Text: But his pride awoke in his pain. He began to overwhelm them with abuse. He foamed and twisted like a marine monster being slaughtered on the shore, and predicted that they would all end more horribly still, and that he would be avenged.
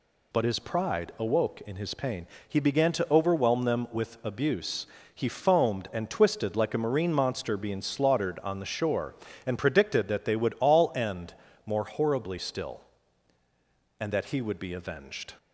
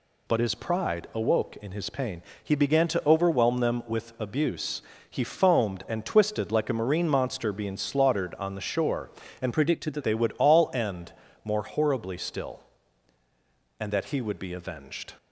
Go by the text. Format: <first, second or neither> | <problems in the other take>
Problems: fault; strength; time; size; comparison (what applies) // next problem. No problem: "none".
first | changes voice from "predicted" to "that"; from 9.5 to 10.0 s; 0.5 s long // pauses between "end" and "more"; slight; at 11.1 s; 0.32 s long; slight in the first